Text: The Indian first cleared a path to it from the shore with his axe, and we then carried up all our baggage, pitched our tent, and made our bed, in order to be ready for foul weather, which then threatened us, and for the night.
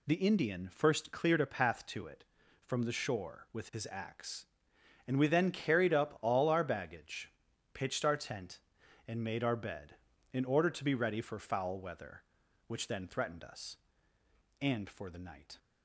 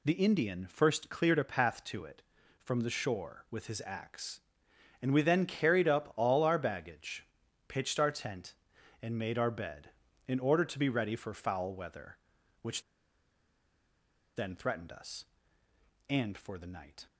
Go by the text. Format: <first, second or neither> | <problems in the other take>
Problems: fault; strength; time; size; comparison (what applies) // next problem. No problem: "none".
first | pauses between "which" and "then"; strong; at 12.8 s; 1.5 s long